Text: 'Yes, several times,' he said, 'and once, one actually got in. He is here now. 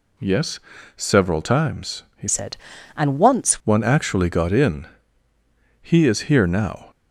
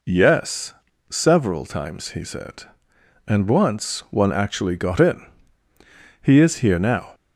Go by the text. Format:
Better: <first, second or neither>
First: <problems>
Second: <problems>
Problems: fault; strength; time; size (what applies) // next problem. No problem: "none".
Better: second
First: changes voice from "said" to "once"; from 2.2 to 3.6 s; 1.4 s long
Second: none